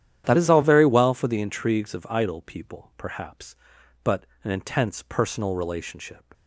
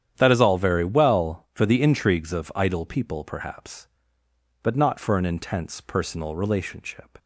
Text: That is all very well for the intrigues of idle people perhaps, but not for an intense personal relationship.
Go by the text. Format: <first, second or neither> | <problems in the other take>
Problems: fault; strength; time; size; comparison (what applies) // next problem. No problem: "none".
second | starts louder than the rest; strong; until 1.2 s; 10.5 dB; strong in the second // skips "not for"; at 4.3 s